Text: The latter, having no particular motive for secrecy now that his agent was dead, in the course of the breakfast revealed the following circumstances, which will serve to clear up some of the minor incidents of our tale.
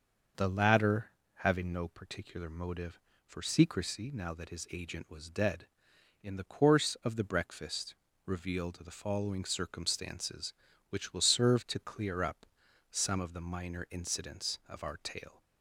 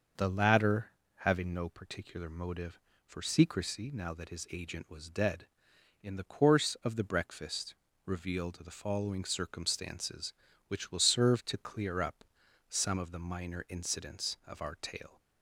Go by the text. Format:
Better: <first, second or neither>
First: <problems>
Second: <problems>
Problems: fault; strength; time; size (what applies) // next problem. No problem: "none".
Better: neither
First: starts louder than the rest; until 1.6 s; 6 dB // pauses between "breakfast" and "revealed"; slight; at 7.9 s; 0.32 s long // pauses between "up" and "some"; at 12.4 s; 0.44 s long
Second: starts louder than the rest; until 1.4 s; 6 dB // pauses between "breakfast" and "revealed"; slight; at 7.7 s; 0.32 s long // pauses between "up" and "some"; at 12.2 s; 0.44 s long